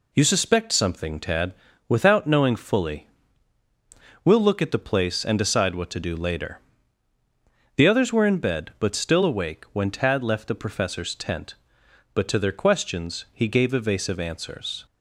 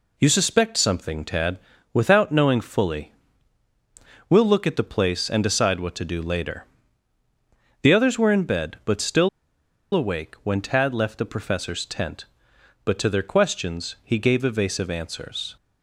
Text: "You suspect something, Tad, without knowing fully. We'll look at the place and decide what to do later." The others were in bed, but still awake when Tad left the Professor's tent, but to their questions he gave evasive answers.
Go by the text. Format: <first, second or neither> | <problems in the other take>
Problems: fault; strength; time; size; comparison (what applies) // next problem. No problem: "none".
first | pauses between "still" and "awake"; noticeable; at 9.2 s; 0.64 s long